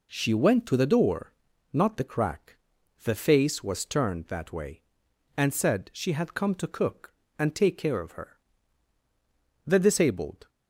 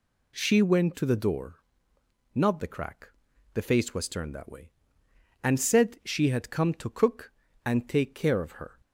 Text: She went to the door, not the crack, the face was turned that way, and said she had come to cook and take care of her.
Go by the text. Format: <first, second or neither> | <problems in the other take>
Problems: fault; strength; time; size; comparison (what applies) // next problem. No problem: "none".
second | goes on to say "The disabled"; noticeable; from 9.6 s on; 0.82 s long